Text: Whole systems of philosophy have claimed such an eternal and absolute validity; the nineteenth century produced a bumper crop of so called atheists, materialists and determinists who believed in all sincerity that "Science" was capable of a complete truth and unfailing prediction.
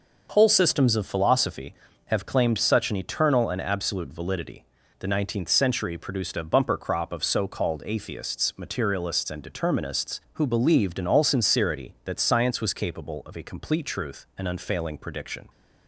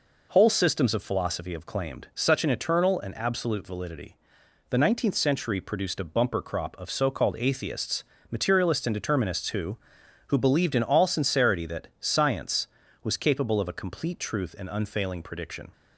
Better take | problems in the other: first | says "who" twice; at 10.2 s

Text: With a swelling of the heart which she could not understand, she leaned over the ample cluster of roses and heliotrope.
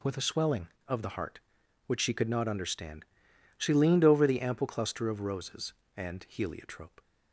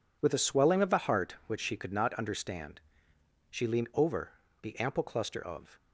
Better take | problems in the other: first | pauses between "over" and "the"; slight; at 4.3 s; 0.28 s long // stops before "roses and heliotrope"; at 5.7 s

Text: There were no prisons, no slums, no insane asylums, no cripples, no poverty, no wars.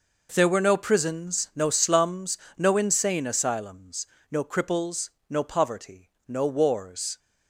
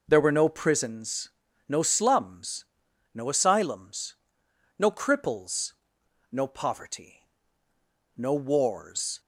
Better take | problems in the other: first | skips "insane"; at 3.2 s

